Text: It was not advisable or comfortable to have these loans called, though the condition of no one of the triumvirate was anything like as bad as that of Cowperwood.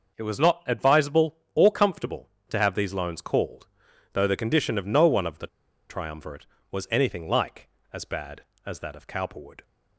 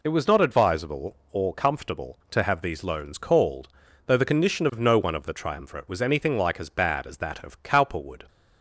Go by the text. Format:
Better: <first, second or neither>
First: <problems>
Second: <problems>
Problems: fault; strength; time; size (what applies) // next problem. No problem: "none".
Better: second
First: starts louder than the rest; noticeable; until 1.2 s; 6 dB // pauses between "the" and "triumvirate"; at 5.4 s; 0.41 s long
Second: none